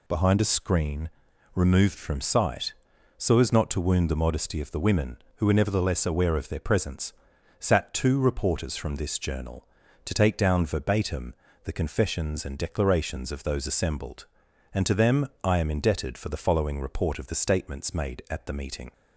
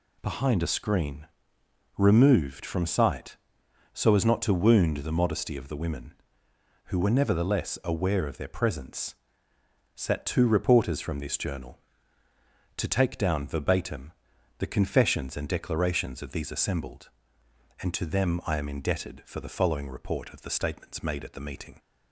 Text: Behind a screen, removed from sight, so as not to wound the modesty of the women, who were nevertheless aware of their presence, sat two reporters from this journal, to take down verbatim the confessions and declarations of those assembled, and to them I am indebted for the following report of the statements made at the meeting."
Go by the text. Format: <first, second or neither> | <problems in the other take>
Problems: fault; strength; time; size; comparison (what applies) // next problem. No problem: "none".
first | pauses between "verbatim" and "the"; noticeable; at 14.1 s; 0.48 s long; slight in the first // says "these" for "those"; at 16.3 s